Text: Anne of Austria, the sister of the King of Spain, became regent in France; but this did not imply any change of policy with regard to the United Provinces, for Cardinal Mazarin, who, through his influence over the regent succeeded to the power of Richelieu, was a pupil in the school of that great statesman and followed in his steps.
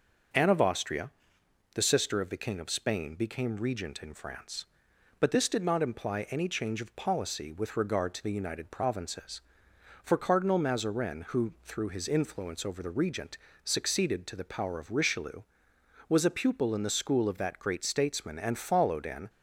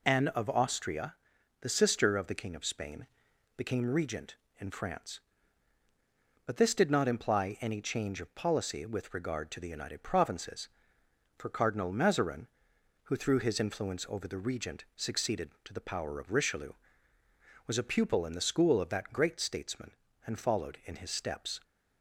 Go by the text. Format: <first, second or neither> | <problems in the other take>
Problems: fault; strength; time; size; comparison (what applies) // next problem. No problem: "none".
second | starts louder than the rest; until 2.0 s; 6 dB // pauses between "regent" and "succeeded"; slight; at 13.3 s; 0.28 s long // stops before "his steps"; at 19.2 s